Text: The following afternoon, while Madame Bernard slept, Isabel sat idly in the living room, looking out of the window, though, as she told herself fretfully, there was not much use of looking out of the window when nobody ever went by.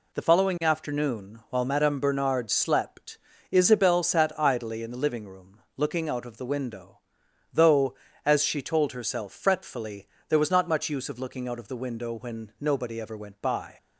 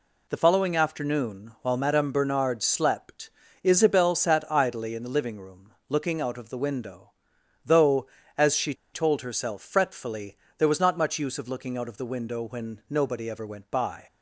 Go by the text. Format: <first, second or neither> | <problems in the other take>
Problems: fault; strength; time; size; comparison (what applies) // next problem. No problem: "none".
first | pauses between "she" and "told"; slight; at 8.7 s; 0.20 s long